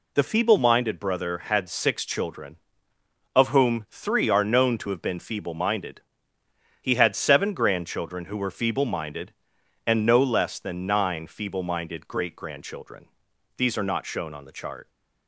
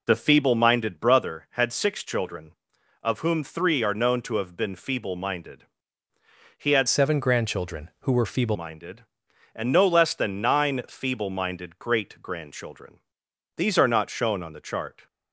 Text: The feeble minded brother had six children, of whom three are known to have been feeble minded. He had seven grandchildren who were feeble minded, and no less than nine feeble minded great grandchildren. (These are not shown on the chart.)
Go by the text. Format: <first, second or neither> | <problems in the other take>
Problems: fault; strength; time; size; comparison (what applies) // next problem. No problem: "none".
first | changes voice from "seven" to "feeble"; from 6.8 to 8.5 s; 1.7 s long